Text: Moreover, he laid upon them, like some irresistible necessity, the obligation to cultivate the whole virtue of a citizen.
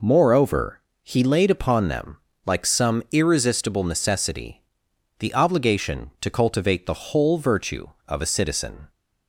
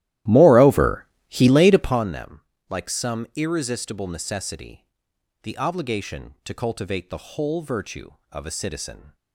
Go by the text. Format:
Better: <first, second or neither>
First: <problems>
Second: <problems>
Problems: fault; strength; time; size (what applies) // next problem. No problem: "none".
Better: first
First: none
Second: starts louder than the rest; strong; until 2.1 s; 14.5 dB